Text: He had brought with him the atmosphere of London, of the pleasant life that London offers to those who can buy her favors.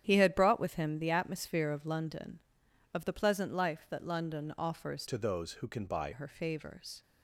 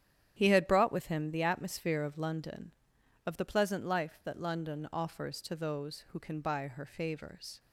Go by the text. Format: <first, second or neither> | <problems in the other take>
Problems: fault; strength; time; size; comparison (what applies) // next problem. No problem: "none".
second | starts louder than the rest; strong; until 1.0 s; 9.5 dB; strong in the second // changes voice from "to" to "buy"; from 5.0 to 6.1 s; 1.1 s long